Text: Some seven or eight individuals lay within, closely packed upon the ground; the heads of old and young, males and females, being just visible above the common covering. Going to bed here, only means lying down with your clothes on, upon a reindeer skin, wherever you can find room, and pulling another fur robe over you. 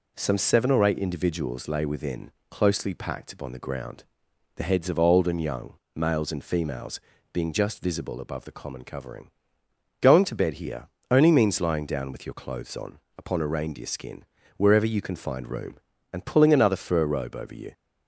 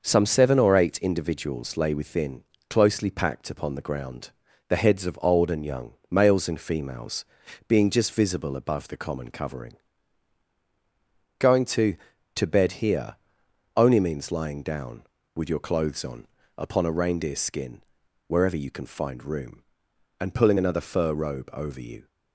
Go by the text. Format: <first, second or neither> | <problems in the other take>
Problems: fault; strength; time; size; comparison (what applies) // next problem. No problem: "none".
first | says "to" twice; at 12.3 s